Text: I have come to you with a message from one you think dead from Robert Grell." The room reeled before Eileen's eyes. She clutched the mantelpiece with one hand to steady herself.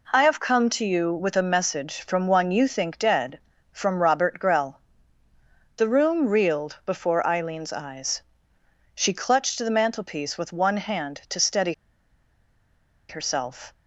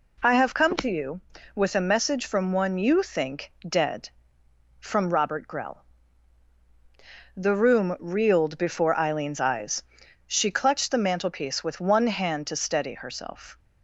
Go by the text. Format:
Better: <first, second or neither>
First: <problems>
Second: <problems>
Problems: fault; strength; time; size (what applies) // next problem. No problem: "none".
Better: second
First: pauses between "steady" and "herself"; strong; at 11.7 s; 1.3 s long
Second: none